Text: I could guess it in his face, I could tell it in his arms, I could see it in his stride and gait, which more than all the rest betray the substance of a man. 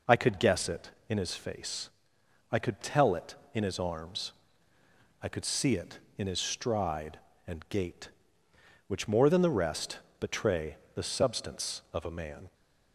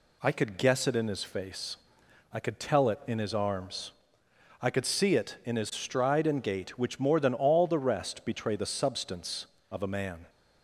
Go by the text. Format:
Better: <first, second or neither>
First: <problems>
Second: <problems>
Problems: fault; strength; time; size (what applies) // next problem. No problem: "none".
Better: second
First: skips "all"; at 9.4 s // pauses between "rest" and "betray"; slight; at 9.9 s; 0.20 s long // pauses between "betray" and "the"; slight; at 10.7 s; 0.20 s long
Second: none